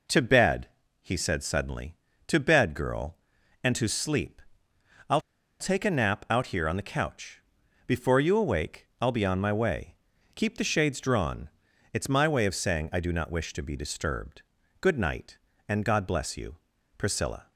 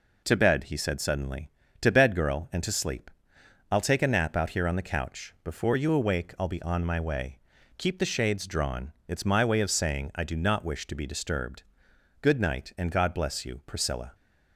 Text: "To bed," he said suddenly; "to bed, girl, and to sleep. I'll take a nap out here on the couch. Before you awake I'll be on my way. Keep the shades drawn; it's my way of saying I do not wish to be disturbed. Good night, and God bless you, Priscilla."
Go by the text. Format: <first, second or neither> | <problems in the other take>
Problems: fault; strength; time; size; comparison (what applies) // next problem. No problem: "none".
second | pauses between "I'll" and "take"; at 5.2 s; 0.39 s long